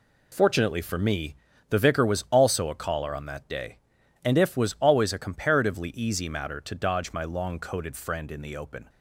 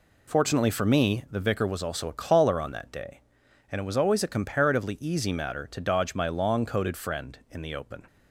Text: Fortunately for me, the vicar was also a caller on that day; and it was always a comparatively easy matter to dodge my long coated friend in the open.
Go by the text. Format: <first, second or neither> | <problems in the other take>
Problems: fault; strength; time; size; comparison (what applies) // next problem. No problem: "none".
second | says "if" for "it"; at 4.3 s